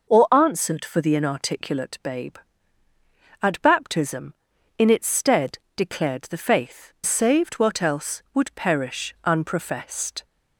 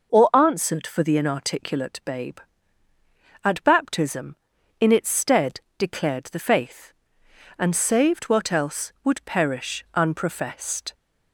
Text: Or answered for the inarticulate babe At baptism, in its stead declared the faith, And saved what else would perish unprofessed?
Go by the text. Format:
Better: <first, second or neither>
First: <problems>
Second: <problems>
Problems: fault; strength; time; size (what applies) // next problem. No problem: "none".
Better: second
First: pauses between "stead" and "declared"; slight; at 5.5 s; 0.18 s long // skips "And"; at 6.9 s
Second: pauses between "stead" and "declared"; slight; at 5.5 s; 0.18 s long